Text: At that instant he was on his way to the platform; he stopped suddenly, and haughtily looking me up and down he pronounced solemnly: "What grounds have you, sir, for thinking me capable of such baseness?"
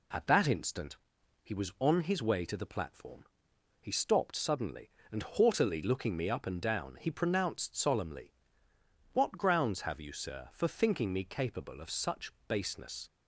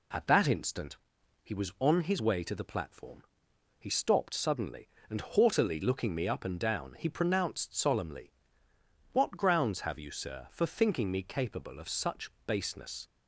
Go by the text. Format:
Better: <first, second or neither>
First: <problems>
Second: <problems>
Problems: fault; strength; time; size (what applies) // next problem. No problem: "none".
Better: neither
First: pauses between "instant" and "he"; at 0.9 s; 0.44 s long // pauses between "such" and "baseness"; slight; at 12.3 s; 0.16 s long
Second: pauses between "instant" and "he"; at 0.9 s; 0.44 s long // pauses between "such" and "baseness"; slight; at 12.3 s; 0.16 s long